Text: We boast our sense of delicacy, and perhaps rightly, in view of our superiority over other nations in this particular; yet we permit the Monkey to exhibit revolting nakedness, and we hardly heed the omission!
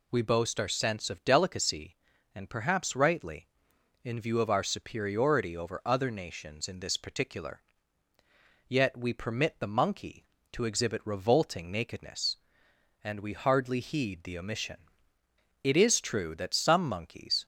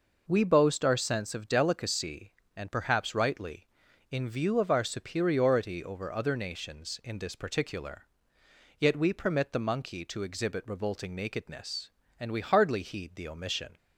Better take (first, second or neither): second